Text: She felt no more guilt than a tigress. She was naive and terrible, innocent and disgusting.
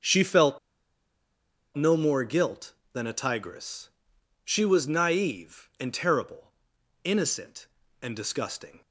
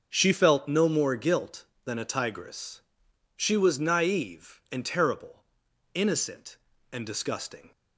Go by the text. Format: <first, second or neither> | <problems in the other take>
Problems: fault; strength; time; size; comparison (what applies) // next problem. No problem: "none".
second | starts louder than the rest; until 2.2 s; 6.5 dB; also in the second // pauses between "felt" and "no"; at 0.5 s; 1.1 s long